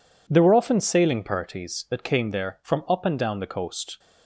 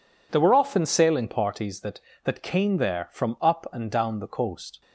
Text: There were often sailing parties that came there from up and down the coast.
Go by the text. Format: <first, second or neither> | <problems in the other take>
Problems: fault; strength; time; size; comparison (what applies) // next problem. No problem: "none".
first | says "that" twice; at 2.2 s